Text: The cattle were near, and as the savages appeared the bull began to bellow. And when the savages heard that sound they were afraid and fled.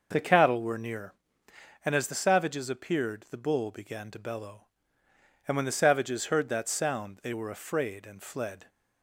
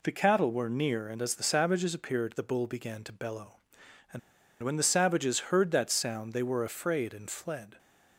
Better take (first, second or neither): first